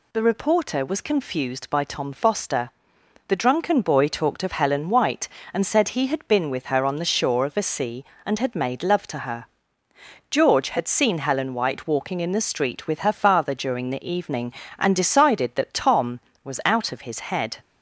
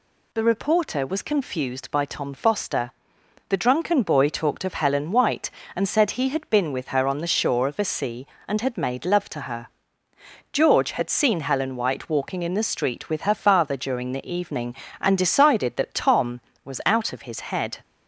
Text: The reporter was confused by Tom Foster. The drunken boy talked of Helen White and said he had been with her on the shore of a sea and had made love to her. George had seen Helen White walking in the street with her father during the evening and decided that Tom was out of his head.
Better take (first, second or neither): neither